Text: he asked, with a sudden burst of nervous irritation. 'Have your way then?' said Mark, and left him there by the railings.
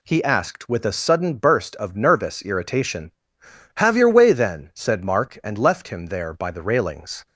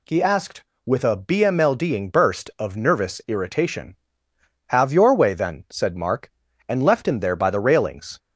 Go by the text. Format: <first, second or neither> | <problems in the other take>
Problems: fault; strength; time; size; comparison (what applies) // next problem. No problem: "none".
first | says "bmlding" for "sudden"; at 1.1 s